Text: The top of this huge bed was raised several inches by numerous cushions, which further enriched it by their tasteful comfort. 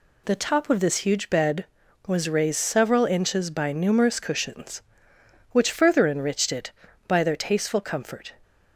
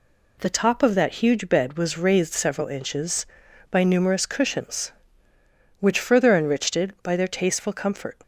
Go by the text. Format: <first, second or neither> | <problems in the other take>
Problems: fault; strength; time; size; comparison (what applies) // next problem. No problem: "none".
first | says "that" for "this"; at 0.9 s